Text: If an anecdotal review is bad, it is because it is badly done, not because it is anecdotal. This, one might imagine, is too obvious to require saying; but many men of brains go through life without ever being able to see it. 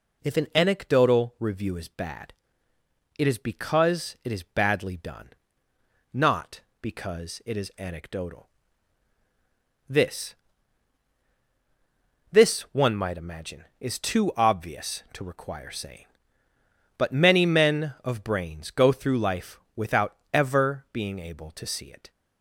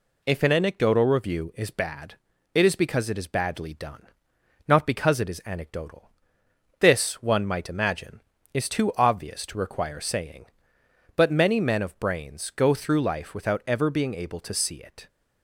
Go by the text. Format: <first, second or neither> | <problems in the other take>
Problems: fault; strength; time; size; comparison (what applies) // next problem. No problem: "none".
second | says "This" twice; at 12.3 s // pauses between "life" and "without"; slight; at 19.5 s; 0.16 s long // pauses between "without" and "ever"; slight; at 20.1 s; 0.16 s long